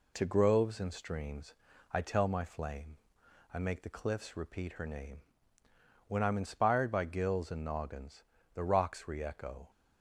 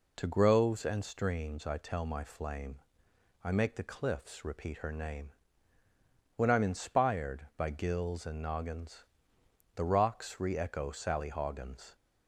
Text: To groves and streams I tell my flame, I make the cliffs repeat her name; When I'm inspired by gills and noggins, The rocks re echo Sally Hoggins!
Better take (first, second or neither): second